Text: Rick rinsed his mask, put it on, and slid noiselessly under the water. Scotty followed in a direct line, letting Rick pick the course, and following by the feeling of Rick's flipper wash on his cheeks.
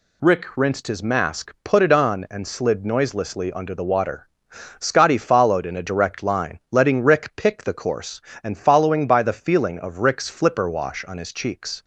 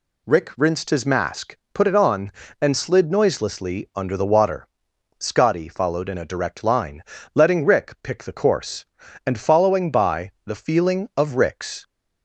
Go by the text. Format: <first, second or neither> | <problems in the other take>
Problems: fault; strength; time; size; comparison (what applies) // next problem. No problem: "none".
first | stops before "flipper wash on his cheeks"; at 11.8 s